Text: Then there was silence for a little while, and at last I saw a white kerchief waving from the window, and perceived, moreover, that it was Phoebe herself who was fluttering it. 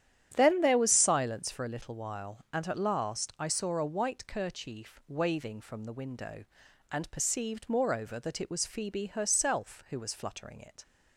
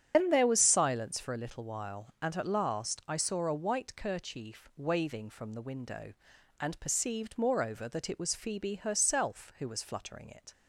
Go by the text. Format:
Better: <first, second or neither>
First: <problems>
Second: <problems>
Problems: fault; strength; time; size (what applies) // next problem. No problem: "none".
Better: first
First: starts louder than the rest; strong; until 1.3 s; 10.5 dB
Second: loses the start of "Then"; at 0.1 s; 145 ms // starts louder than the rest; strong; until 1.1 s; 9.5 dB